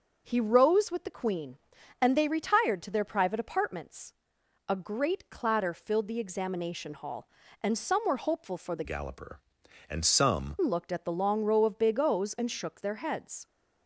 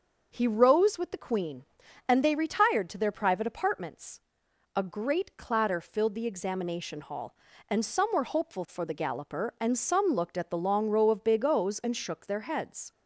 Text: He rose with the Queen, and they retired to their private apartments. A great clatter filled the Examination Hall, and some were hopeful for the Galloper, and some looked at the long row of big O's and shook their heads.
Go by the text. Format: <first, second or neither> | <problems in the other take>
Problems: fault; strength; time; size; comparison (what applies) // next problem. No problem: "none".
second | starts louder than the rest; until 1.2 s; 6.5 dB; also in the second // changes voice from "Galloper" to "some"; from 8.8 to 10.5 s; 1.7 s long